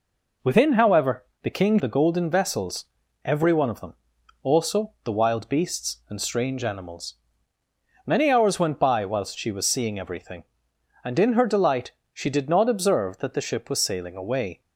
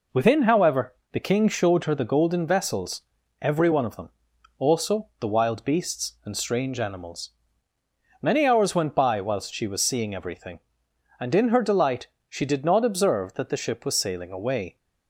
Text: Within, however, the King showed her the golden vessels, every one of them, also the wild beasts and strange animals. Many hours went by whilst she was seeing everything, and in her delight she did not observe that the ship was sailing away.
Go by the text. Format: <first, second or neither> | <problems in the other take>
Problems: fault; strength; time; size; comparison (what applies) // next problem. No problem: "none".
second | skips "showed her"; at 1.7 s // pauses between "delight" and "she"; slight; at 11.9 s; 0.20 s long; slight in the second